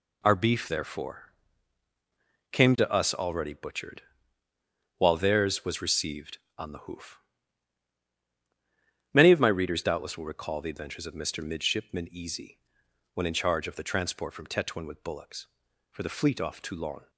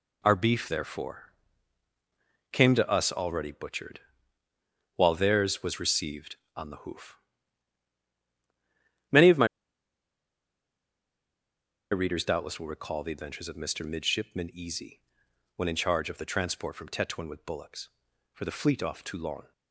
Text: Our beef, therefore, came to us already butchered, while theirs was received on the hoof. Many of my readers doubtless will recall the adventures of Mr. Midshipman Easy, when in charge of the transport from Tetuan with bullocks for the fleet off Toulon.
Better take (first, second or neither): first